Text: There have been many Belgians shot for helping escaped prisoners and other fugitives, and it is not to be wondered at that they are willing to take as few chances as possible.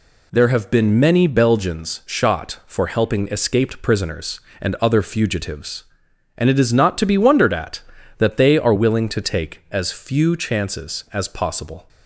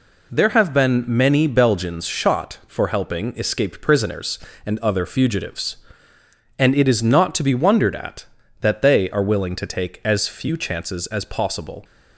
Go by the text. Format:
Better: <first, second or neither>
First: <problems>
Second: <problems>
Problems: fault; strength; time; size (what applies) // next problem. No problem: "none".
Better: neither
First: none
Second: none